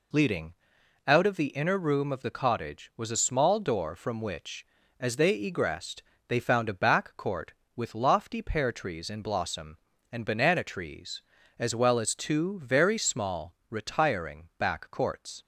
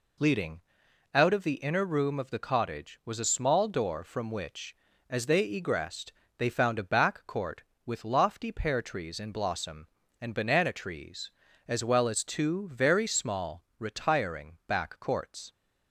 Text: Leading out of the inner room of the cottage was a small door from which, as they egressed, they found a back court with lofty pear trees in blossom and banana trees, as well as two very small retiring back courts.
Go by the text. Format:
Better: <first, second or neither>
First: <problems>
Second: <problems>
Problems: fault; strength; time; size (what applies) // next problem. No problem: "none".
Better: neither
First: pauses between "Leading" and "out"; noticeable; at 0.5 s; 0.56 s long // pauses between "small" and "retiring"; slight; at 13.5 s; 0.16 s long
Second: pauses between "Leading" and "out"; noticeable; at 0.5 s; 0.56 s long // pauses between "small" and "retiring"; slight; at 13.6 s; 0.16 s long